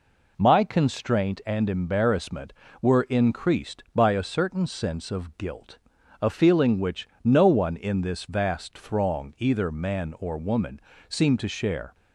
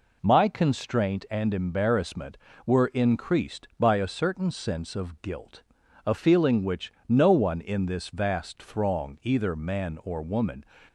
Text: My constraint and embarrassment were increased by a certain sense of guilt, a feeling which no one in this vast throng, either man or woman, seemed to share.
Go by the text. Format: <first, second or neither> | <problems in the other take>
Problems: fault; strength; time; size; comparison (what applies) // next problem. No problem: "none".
first | pauses between "which" and "no"; slight; at 6.9 s; 0.16 s long; slight in the first // stops before "seemed to share"; at 10.8 s